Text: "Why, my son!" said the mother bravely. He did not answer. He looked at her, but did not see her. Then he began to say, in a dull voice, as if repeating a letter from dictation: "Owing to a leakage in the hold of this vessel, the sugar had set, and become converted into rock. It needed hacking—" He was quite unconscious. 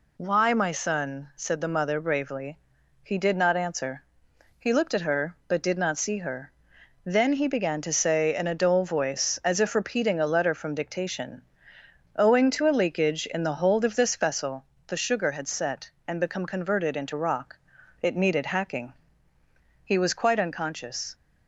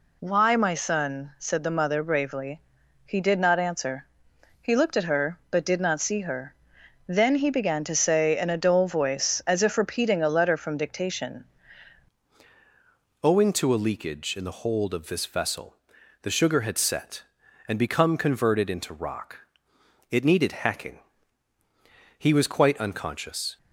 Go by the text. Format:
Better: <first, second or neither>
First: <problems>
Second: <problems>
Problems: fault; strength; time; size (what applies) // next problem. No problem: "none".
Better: first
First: none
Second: changes voice at "Owing"; from 13.2 s on; 10.3 s long